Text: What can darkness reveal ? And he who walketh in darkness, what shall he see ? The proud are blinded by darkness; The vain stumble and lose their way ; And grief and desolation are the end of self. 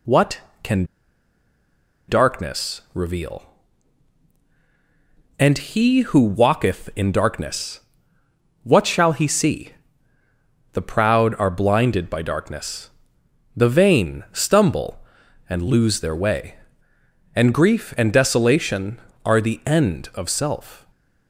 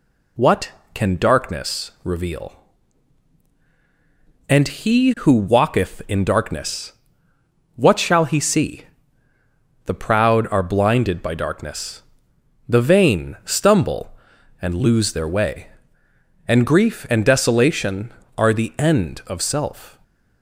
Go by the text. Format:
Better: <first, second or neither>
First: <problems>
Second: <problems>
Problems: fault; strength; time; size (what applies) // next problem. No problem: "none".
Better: second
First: pauses between "can" and "darkness"; at 0.8 s; 1.2 s long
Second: none